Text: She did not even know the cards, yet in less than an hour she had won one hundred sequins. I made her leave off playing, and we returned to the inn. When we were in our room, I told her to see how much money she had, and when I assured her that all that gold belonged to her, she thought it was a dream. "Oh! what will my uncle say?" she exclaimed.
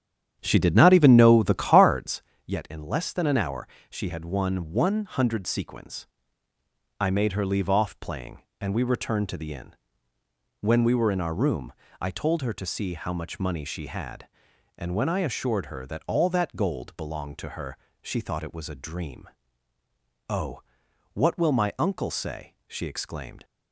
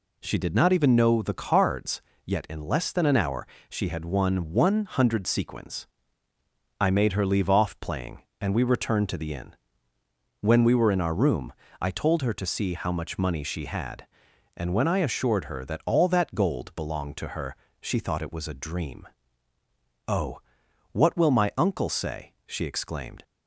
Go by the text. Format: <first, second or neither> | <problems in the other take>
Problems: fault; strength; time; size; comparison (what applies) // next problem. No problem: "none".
second | starts louder than the rest; strong; until 2.2 s; 9.5 dB // pauses between "hour" and "she"; slight; at 3.6 s; 0.22 s long; slight in the second